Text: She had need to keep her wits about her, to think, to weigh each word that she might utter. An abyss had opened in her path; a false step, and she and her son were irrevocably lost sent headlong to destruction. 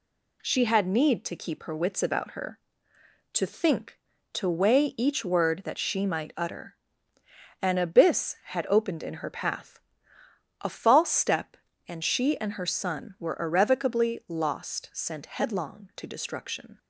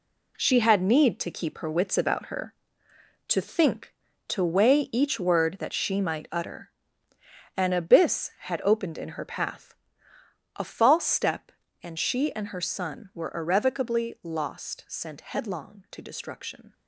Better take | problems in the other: first | gets quieter; strong; throughout; 9 dB

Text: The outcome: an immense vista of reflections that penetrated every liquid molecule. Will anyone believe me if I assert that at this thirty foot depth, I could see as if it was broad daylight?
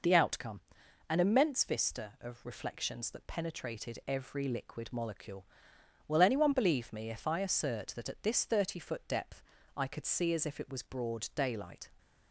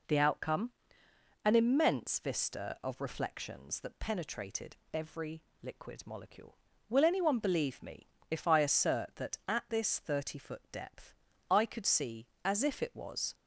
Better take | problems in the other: first | pauses between "penetrated" and "every"; slight; at 4.7 s; 0.16 s long // pauses between "every" and "liquid"; slight; at 5.4 s; 0.18 s long // pauses between "me" and "if"; slight; at 8.0 s; 0.22 s long // stops before "broad daylight"; at 13.3 s

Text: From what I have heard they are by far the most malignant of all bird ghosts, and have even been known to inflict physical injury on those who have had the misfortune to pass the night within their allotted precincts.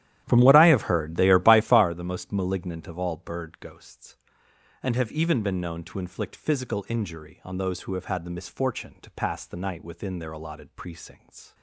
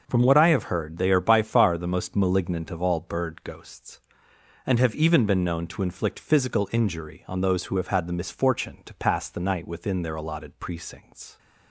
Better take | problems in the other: second | starts louder than the rest; strong; until 2.0 s; 12 dB

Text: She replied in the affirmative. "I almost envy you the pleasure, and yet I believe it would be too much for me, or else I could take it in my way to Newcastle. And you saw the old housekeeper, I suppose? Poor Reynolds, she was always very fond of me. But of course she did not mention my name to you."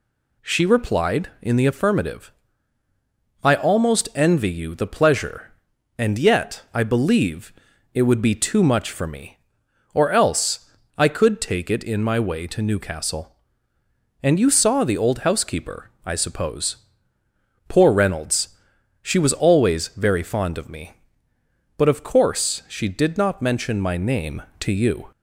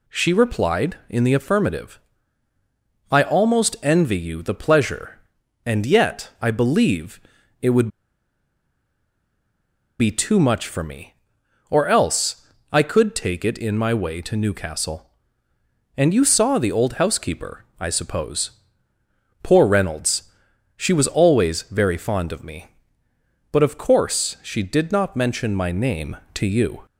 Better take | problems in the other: first | pauses between "believe" and "it"; at 7.2 s; 0.40 s long; also in the first // pauses between "would" and "be"; strong; at 7.8 s; 2.1 s long // pauses between "else" and "I"; slight; at 12.4 s; 0.24 s long; slight in the first

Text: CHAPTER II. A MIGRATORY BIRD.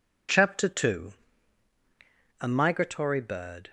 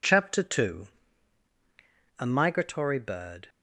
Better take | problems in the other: neither | none

